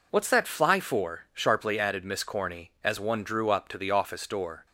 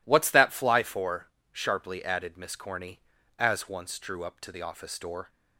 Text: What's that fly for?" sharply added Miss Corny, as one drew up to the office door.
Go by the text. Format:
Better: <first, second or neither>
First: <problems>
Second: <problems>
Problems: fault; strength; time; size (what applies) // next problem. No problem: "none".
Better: first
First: none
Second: says "once" for "one"; at 3.6 s